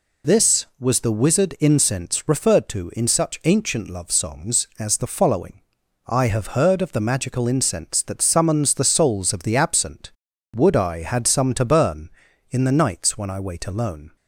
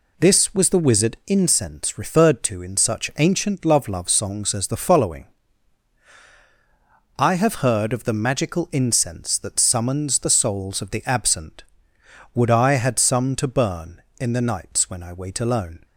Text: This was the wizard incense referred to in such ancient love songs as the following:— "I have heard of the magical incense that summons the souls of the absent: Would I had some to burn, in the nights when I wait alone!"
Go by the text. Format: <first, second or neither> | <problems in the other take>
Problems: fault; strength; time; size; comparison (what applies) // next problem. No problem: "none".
first | says "love" twice; at 3.8 s